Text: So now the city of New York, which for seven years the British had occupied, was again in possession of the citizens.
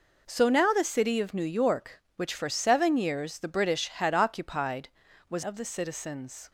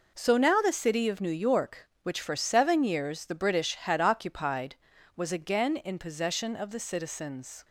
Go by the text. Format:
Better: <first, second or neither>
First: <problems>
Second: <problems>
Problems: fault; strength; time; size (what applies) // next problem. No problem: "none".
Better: second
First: skips "again in possession"; at 5.4 s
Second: none